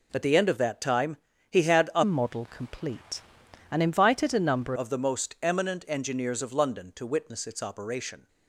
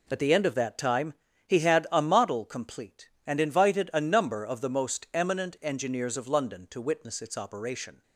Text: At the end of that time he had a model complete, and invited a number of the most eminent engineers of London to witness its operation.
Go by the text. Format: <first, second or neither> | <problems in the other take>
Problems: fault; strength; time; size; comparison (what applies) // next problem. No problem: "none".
second | pauses between "time" and "he"; slight; at 1.1 s; 0.32 s long; slight in the second // changes voice from "model" to "number"; from 2.0 to 4.7 s; 2.7 s long